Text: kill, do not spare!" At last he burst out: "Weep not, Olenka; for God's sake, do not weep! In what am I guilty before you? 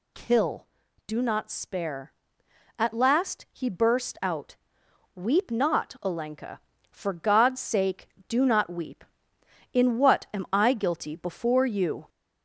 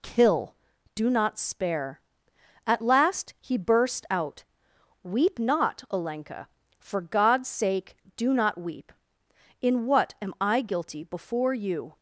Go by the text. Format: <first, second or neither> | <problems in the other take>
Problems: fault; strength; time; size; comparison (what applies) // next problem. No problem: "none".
second | gets louder; throughout; 3.5 dB